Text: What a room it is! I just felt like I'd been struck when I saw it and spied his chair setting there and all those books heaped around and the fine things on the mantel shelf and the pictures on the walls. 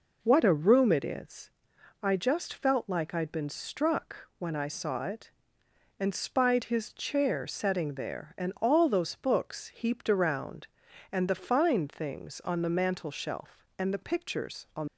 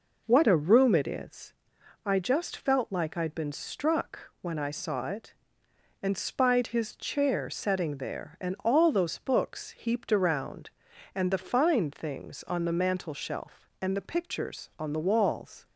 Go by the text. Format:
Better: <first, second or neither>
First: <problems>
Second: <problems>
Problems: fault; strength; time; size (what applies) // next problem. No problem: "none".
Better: second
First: stops before "the walls"; at 14.8 s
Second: none